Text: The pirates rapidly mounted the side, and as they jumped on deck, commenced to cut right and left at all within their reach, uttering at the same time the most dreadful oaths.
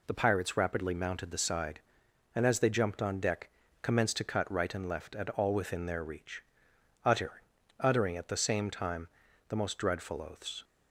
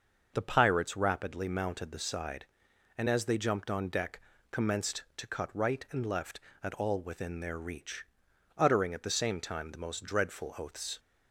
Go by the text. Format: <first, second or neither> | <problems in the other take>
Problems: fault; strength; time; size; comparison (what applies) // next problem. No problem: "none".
second | says "uttering" twice; at 7.7 s // pauses between "time" and "the"; at 9.0 s; 0.40 s long